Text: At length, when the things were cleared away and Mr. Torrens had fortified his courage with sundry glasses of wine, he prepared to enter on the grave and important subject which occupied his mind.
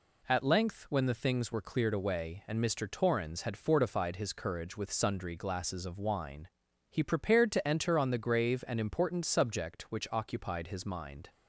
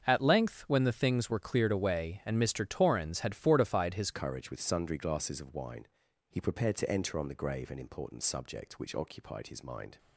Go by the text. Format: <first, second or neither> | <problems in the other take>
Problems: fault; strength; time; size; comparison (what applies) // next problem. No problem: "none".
first | starts louder than the rest; until 1.0 s; 7 dB // changes voice at "courage"; from 4.1 s on; 5.8 s long